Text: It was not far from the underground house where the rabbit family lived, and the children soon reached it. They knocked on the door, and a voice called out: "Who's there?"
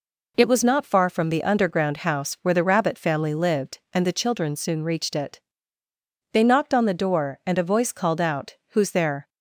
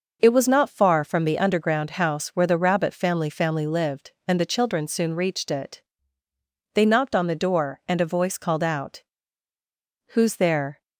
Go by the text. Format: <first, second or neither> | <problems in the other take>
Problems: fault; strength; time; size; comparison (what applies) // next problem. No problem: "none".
first | says "family" twice; at 3.2 s